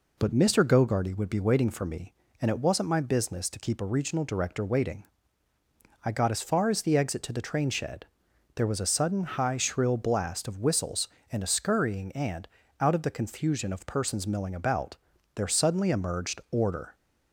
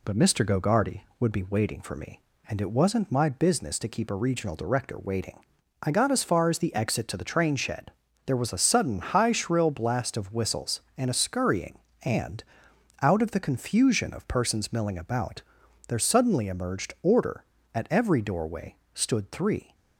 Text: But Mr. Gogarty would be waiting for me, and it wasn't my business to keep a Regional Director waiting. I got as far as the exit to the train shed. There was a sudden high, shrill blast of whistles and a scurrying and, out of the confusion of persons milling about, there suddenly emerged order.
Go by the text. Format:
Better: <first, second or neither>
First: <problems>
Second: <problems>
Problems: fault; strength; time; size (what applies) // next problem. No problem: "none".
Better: first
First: none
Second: goes on to say "At every doorway stood three"; strong; from 17.7 s on; 1.9 s long